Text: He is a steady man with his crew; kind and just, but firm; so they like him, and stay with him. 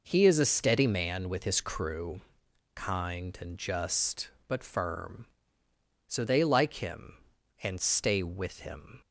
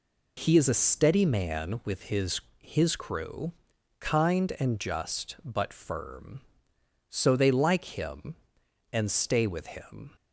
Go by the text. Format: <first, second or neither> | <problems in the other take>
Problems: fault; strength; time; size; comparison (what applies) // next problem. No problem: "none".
first | says "his" twice; at 2.6 s